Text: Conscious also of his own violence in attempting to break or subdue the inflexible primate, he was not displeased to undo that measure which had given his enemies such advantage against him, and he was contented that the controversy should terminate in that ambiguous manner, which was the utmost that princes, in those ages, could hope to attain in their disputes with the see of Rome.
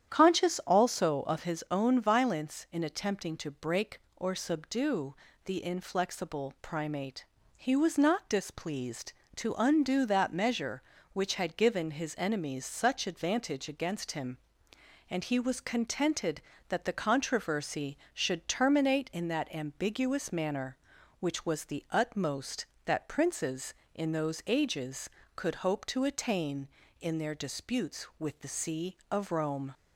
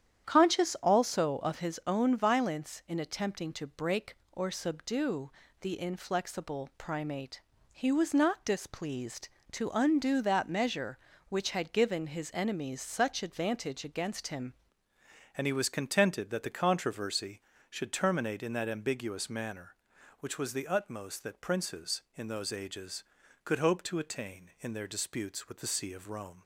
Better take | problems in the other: first | starts louder than the rest; strong; until 1.2 s; 10 dB; strong in the first // pauses between "subdue" and "the"; slight; at 5.3 s; 0.30 s long; slight in the first // changes voice at "and"; from 15.3 s on; 11.1 s long

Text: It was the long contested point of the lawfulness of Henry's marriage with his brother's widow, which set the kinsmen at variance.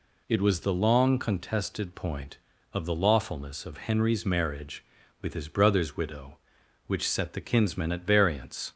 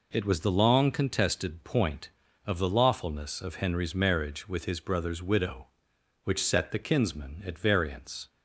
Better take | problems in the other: neither | none

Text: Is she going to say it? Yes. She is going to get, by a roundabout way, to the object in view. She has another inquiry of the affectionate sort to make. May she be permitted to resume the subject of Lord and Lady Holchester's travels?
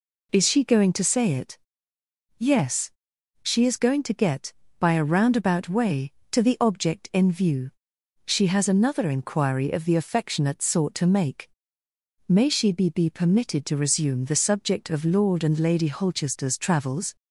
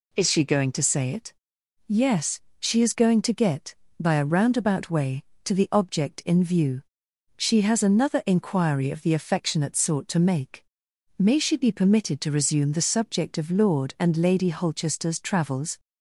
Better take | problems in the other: second | says "be" twice; at 12.8 s

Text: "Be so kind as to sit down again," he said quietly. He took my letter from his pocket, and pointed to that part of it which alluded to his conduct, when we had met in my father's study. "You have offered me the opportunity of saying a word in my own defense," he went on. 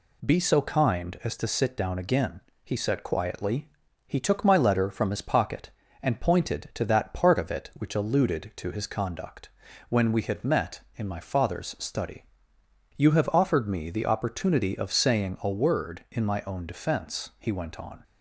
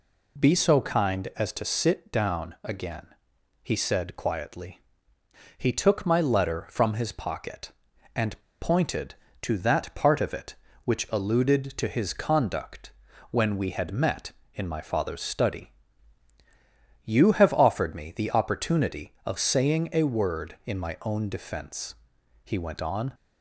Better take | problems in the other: first | pauses between "and" and "pointed"; slight; at 8.3 s; 0.21 s long

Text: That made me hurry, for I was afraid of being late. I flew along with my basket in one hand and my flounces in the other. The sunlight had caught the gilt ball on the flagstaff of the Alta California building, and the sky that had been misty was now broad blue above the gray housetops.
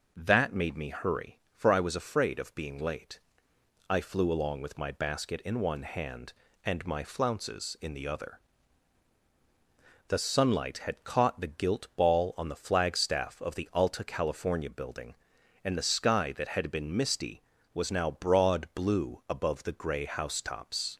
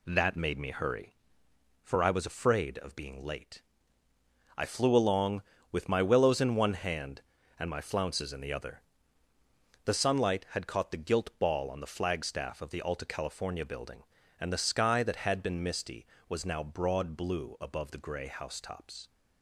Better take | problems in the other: first | says "willows" for "basket"; at 6.0 s

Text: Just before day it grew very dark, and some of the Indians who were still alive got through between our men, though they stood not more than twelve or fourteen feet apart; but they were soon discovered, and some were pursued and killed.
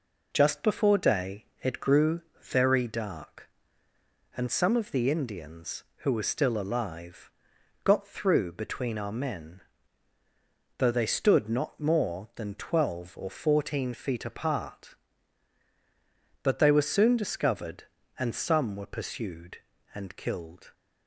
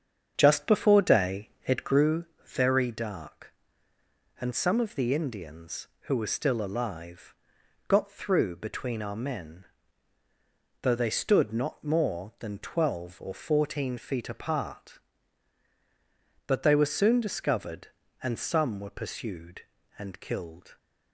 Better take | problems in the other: first | starts louder than the rest; strong; until 2.0 s; 7.5 dB // pauses between "day" and "it"; slight; at 1.4 s; 0.16 s long; slight in the first // pauses between "grew" and "very"; slight; at 2.2 s; 0.20 s long; slight in the first // pauses between "alive" and "got"; noticeable; at 7.3 s; 0.54 s long; noticeable in the first

